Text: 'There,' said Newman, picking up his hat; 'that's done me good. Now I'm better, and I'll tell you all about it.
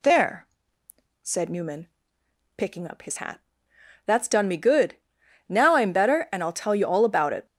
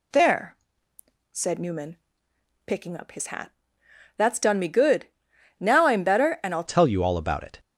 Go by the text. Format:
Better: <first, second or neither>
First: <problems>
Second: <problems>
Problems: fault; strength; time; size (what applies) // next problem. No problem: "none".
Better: first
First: none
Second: changes voice at "tell"; from 6.6 s on; 0.9 s long